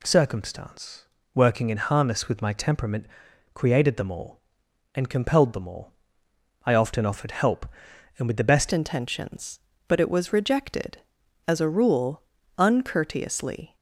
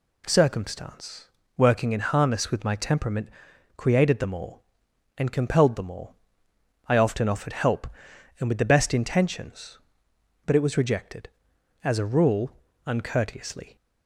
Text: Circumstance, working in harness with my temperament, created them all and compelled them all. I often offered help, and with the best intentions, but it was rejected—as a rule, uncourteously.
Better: second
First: changes voice at "intentions"; from 8.7 s on; 5.0 s long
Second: none

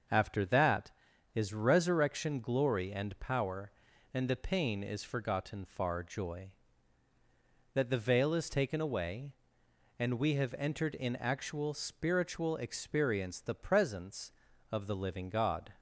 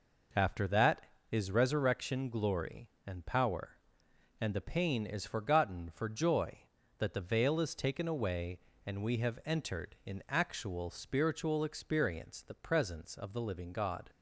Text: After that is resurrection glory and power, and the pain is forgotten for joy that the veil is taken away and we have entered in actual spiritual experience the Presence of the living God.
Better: second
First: starts louder than the rest; until 1.5 s; 6.5 dB // says "far" for "for"; at 5.6 s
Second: none

